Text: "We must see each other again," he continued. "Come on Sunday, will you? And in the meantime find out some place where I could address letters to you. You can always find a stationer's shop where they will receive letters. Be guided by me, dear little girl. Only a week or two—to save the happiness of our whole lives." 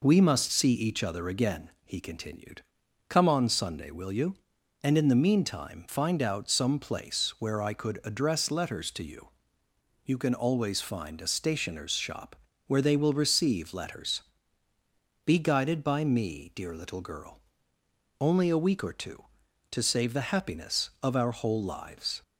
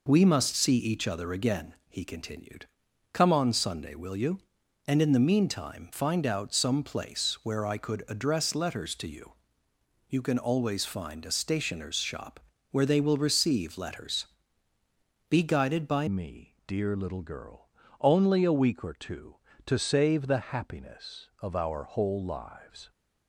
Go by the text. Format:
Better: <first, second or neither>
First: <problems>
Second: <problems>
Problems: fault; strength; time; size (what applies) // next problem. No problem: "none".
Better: first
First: pauses between "shop" and "where"; slight; at 12.3 s; 0.32 s long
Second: pauses between "shop" and "where"; slight; at 12.3 s; 0.32 s long // changes voice at "me"; from 16.0 s on; 6.9 s long